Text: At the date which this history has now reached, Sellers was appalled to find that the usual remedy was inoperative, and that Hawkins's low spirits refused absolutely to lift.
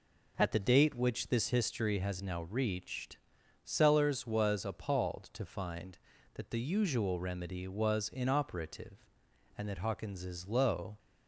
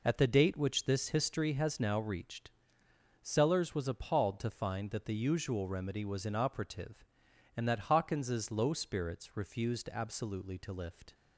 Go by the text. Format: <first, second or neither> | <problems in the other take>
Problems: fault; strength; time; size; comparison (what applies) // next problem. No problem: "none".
second | stops before "spirits refused absolutely to lift"; at 10.9 s